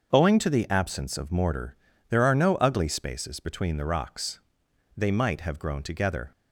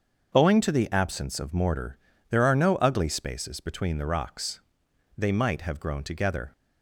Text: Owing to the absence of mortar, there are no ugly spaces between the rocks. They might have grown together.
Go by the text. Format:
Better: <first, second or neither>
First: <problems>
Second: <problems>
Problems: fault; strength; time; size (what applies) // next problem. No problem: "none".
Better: neither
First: starts louder than the rest; until 1.1 s; 6.5 dB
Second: starts louder than the rest; until 1.3 s; 6.5 dB